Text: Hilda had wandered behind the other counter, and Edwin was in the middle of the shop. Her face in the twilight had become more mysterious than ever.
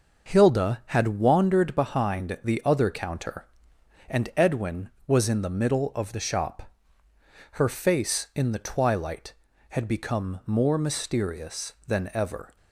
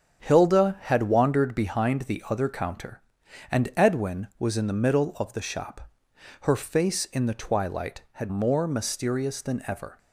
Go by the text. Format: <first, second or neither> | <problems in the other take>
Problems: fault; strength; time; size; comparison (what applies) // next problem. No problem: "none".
first | starts louder than the rest; strong; until 1.2 s; 8.5 dB // skips "become"; at 8.2 s